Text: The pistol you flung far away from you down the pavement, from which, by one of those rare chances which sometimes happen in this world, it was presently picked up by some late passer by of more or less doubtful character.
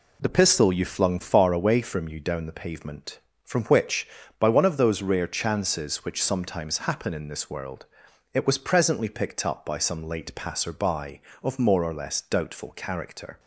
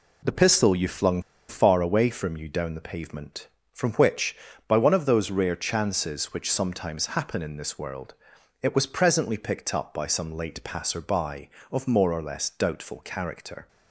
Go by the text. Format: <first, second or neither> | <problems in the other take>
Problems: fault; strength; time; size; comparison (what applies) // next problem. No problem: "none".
first | pauses between "flung" and "far"; slight; at 1.1 s; 0.29 s long